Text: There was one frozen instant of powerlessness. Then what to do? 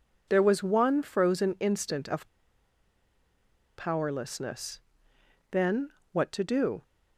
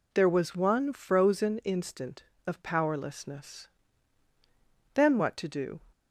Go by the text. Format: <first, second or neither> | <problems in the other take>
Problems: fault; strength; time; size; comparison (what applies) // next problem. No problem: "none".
second | pauses between "of" and "powerlessness"; strong; at 2.2 s; 1.5 s long // pauses between "Then" and "what"; slight; at 5.8 s; 0.24 s long